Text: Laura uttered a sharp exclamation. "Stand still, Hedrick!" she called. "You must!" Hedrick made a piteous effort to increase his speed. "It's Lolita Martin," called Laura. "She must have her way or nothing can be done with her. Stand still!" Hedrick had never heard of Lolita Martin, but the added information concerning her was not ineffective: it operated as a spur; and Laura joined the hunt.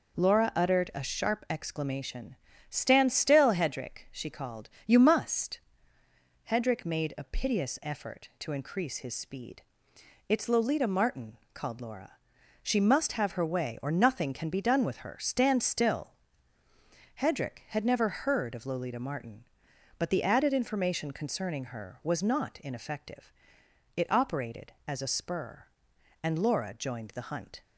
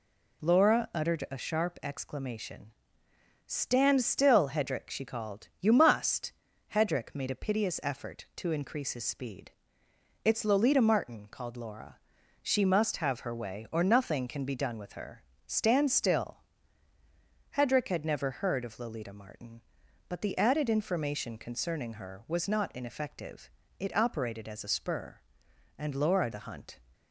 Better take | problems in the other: first | skips "joined"; at 26.3 s

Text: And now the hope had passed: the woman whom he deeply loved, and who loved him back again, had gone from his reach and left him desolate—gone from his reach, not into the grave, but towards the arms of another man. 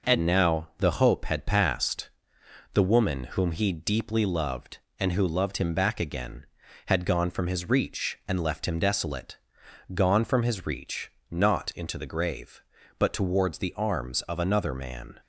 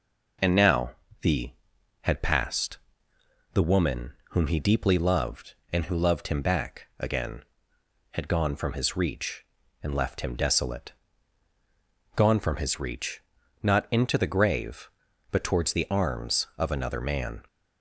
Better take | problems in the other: first | pauses between "now" and "the"; slight; at 0.9 s; 0.28 s long // skips "hope"; at 1.7 s // pauses between "woman" and "whom"; slight; at 4.1 s; 0.16 s long

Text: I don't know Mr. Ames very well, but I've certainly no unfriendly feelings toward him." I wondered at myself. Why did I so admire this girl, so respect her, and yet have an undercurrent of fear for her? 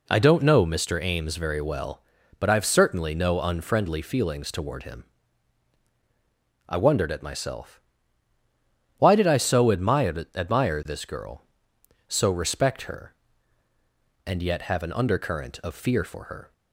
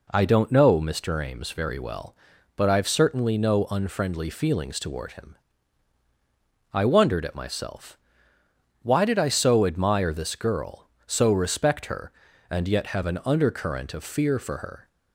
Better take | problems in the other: second | says "admire" twice; at 10.3 s

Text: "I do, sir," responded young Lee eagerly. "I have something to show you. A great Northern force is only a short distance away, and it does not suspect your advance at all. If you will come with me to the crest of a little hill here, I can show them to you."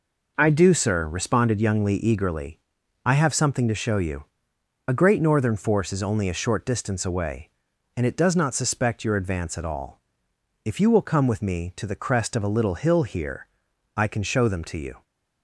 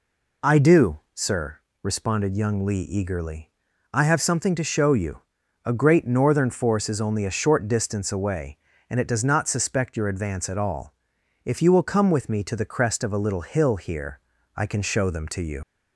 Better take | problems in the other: first | leaves "you" unfinished; at 15.6 s; 65 ms

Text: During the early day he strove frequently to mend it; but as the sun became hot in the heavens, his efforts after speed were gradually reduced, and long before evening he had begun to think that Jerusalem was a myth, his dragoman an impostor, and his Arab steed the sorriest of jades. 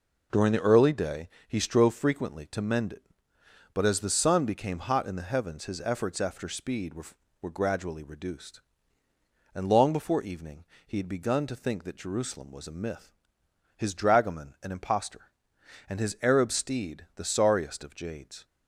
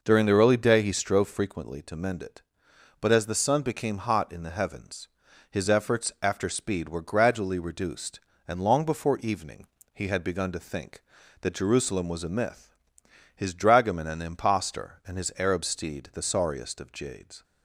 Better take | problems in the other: second | pauses between "day" and "he"; slight; at 1.2 s; 0.18 s long // says "were" twice; at 7.4 s // pauses between "evening" and "he"; slight; at 10.6 s; 0.24 s long; slight in the second

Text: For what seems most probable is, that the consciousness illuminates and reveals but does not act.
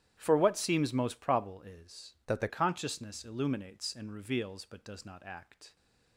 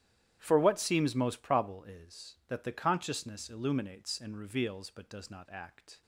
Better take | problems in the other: second | starts louder than the rest; strong; until 1.1 s; 11.5 dB; strong in the second // changes voice from "that" to "the"; from 2.2 to 2.4 s; 0.2 s long

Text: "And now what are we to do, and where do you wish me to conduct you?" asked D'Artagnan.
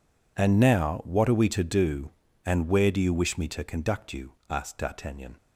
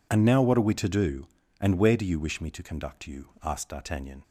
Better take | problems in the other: neither | none

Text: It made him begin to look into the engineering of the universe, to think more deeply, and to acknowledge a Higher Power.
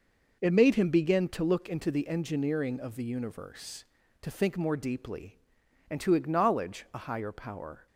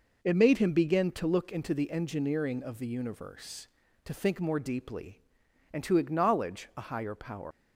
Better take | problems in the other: first | leaves "Power" unfinished; at 7.5 s; 185 ms

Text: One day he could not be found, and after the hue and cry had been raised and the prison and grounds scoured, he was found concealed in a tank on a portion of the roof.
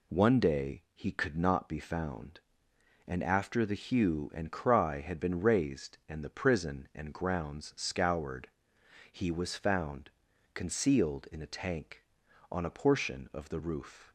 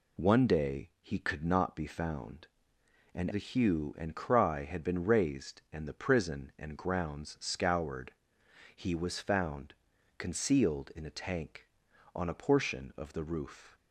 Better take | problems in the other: first | skips "after"; at 3.2 s // pauses between "found" and "concealed"; noticeable; at 9.7 s; 0.46 s long; noticeable in the first

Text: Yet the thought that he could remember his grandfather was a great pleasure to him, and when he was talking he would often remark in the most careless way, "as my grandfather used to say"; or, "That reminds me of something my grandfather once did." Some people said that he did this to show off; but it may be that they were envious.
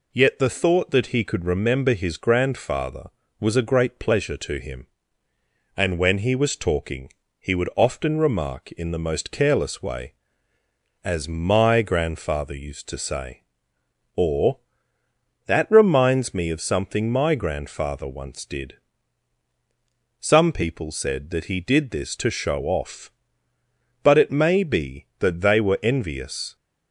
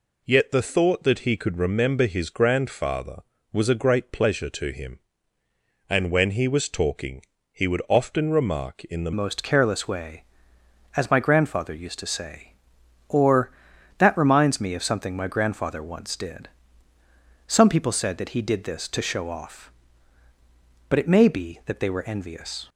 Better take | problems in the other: first | pauses between "talking" and "he"; slight; at 7.2 s; 0.28 s long; slight in the first // changes voice at "most"; from 9.1 s on; 13.5 s long

